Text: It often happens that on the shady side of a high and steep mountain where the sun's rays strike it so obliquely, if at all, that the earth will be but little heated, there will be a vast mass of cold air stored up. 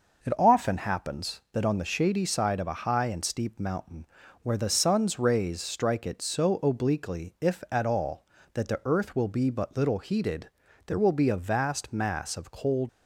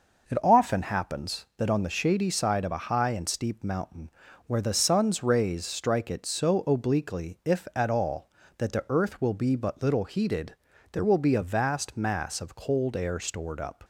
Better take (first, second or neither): second